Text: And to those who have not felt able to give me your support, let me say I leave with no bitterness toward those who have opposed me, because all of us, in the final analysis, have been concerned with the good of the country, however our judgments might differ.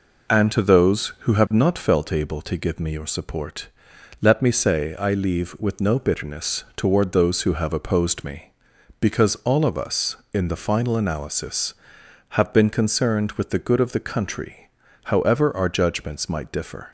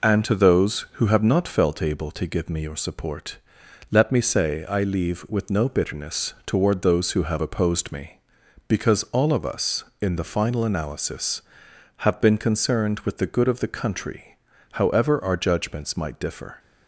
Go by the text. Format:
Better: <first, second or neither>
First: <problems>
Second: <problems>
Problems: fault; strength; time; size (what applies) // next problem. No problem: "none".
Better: neither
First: none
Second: none